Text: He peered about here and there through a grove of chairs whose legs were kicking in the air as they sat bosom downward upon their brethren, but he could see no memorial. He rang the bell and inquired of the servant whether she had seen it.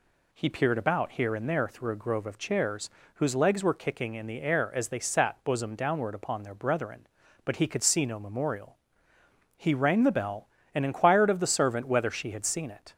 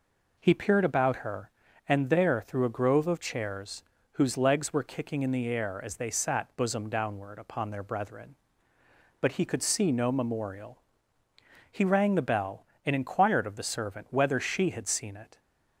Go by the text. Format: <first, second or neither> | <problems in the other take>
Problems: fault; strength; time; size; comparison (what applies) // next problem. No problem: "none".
first | says "her" for "here"; at 1.1 s // pauses between "chairs" and "whose"; slight; at 3.8 s; 0.30 s long; slight in the first